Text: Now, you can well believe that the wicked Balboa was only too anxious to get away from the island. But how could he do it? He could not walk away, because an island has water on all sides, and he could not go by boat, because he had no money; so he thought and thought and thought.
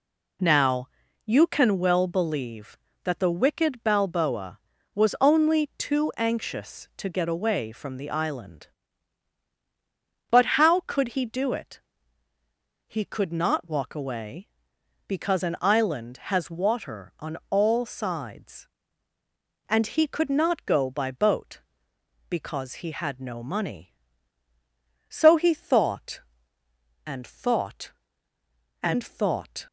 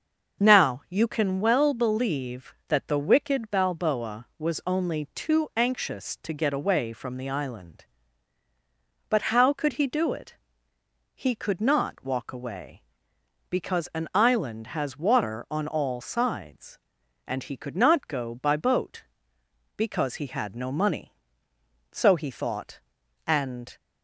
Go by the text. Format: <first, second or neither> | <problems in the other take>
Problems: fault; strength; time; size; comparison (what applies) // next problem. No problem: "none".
first | starts louder than the rest; until 1.4 s; 6.5 dB // stops before "thought and thought"; at 23.7 s